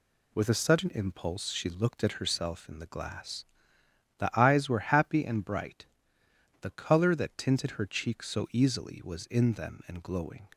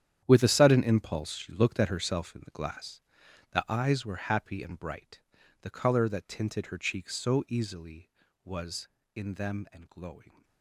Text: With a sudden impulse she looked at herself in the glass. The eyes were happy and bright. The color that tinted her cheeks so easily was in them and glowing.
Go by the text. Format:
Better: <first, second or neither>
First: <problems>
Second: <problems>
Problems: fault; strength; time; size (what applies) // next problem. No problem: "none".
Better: first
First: none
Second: gets quieter; strong; throughout; 14 dB